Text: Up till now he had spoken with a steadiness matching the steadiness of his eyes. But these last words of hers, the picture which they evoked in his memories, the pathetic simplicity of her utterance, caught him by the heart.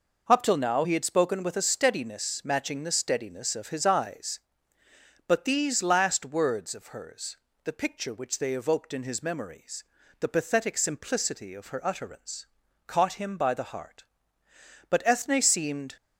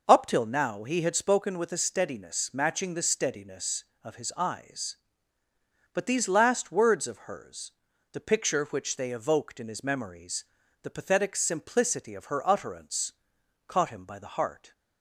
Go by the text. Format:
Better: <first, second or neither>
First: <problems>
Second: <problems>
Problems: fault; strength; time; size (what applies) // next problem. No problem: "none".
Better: second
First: goes on to say "But Ethne seemed"; noticeable; from 14.9 s on; 1.0 s long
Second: none